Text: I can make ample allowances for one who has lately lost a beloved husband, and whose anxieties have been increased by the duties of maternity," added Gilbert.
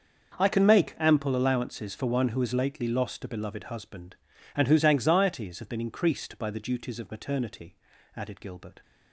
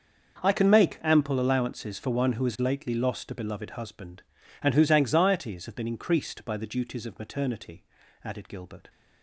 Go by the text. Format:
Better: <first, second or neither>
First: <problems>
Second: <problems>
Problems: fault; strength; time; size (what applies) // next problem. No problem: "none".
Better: neither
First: starts louder than the rest; until 1.4 s; 6.5 dB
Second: starts louder than the rest; until 1.4 s; 6.5 dB